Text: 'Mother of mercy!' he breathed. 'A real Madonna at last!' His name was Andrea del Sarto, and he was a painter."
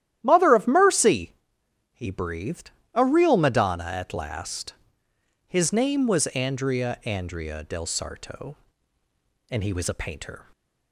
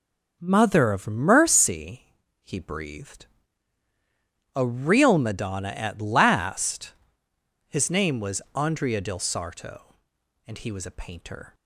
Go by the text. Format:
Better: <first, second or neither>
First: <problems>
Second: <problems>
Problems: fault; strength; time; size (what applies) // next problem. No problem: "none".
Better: second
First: starts louder than the rest; strong; until 1.2 s; 12 dB // says "Andrea" twice; at 7.0 s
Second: none